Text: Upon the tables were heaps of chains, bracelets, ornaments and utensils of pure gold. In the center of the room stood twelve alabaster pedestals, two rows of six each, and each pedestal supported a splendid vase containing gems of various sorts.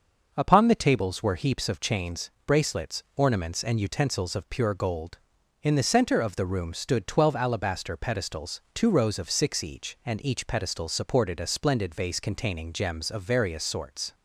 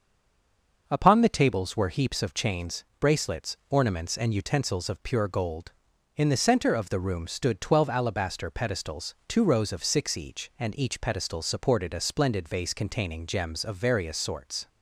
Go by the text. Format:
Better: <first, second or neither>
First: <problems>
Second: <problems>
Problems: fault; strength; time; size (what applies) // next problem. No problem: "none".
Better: first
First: starts louder than the rest; until 1.3 s; 6 dB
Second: stays silent before the first word; slight; until 0.8 s; 0.8 s long // starts louder than the rest; until 1.8 s; 6 dB